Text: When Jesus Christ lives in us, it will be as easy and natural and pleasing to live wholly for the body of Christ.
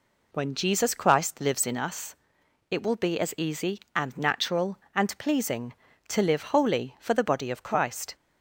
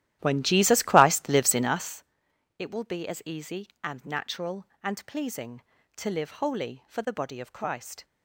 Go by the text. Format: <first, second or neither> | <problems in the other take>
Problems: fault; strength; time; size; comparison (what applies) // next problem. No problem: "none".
first | starts louder than the rest; strong; until 2.1 s; 13.5 dB